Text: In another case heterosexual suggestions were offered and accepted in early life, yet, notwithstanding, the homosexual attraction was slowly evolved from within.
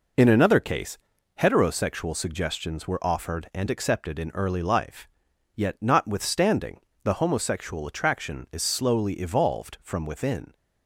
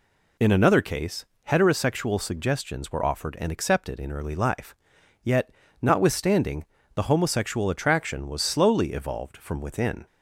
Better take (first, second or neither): second